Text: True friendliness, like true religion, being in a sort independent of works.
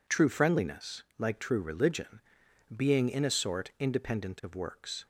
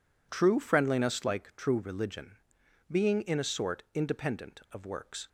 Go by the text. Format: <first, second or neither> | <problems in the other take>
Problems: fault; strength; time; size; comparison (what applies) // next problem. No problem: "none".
neither | none